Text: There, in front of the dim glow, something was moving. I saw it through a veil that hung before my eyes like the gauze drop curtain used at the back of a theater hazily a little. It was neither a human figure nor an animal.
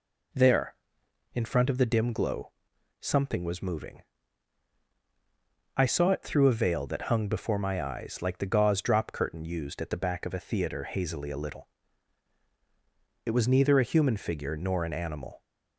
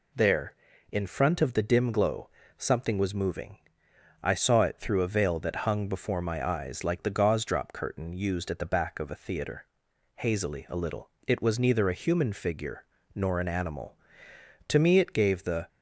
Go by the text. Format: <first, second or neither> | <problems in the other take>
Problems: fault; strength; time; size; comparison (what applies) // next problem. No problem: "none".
first | pauses between "theater" and "hazily"; noticeable; at 9.6 s; 0.52 s long // pauses between "figure" and "nor"; slight; at 12.8 s; 0.30 s long // goes on to say "To me it gave the"; noticeable; from 14.6 s on; 0.98 s long